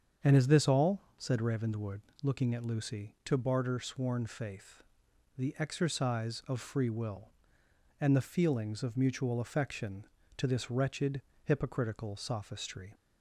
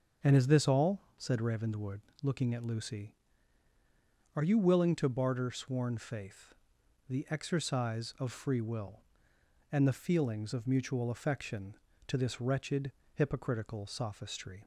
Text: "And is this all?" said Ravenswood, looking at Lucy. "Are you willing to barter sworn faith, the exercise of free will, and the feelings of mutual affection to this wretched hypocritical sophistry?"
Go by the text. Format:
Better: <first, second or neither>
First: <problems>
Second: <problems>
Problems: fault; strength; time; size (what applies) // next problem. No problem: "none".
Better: second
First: starts louder than the rest; strong; until 1.4 s; 7.5 dB // skips "Are you willing"; at 3.1 s // pauses between "wretched" and "hypocritical"; slight; at 11.1 s; 0.24 s long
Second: starts louder than the rest; until 1.4 s; 6.5 dB // pauses between "wretched" and "hypocritical"; slight; at 12.8 s; 0.24 s long